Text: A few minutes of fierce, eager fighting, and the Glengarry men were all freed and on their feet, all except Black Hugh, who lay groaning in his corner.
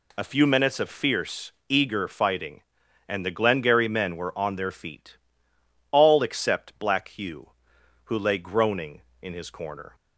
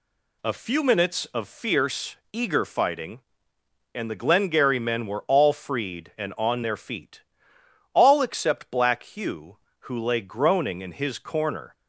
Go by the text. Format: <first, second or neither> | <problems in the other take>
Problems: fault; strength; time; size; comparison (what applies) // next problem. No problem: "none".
second | skips "all freed and"; at 4.3 s